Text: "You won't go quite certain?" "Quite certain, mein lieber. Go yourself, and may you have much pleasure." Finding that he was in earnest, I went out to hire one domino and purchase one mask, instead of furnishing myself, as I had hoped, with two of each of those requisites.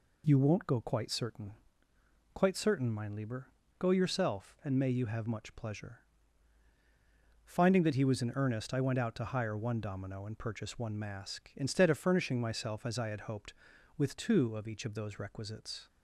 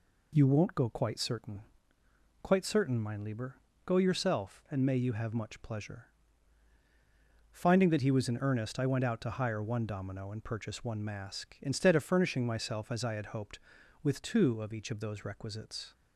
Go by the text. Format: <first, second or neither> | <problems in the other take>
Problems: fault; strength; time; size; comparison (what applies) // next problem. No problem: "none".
neither | none